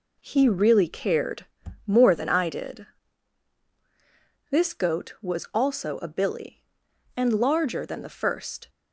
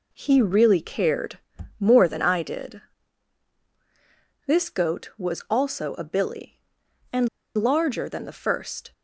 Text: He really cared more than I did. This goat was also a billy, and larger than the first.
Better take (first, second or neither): first